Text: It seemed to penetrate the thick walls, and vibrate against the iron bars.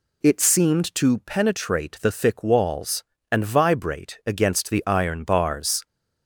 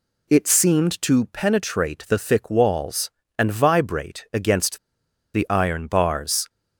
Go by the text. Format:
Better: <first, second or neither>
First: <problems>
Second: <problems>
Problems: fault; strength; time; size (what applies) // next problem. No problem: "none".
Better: first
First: none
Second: pauses between "against" and "the"; noticeable; at 4.7 s; 0.58 s long